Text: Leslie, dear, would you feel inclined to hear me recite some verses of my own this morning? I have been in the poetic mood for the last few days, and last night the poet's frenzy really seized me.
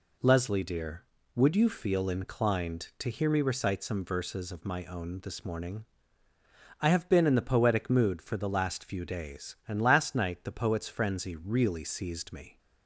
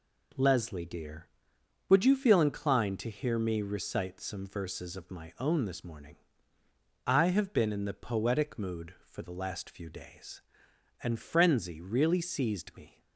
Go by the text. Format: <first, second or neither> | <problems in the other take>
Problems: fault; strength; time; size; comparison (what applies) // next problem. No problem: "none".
first | skips "last night the poet's"; at 11.1 s